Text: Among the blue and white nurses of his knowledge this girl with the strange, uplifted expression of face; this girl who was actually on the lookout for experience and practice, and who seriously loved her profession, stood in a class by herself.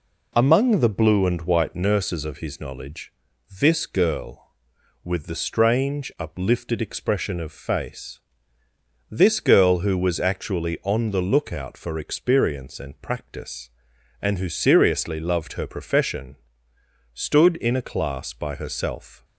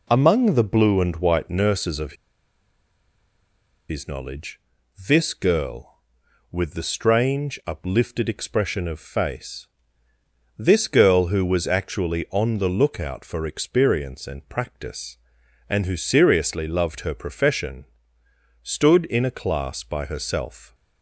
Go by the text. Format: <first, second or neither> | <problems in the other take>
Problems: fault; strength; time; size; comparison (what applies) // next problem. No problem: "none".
first | pauses between "of" and "his"; strong; at 2.1 s; 1.7 s long // pauses between "knowledge" and "this"; noticeable; at 4.6 s; 0.48 s long; noticeable in the first